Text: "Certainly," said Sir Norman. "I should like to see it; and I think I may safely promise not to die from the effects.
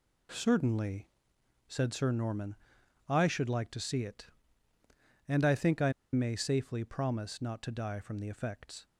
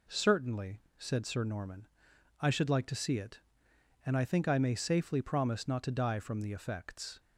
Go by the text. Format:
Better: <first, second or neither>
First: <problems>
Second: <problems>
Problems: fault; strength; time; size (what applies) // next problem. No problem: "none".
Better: second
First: pauses between "I" and "may"; slight; at 5.9 s; 0.20 s long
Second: none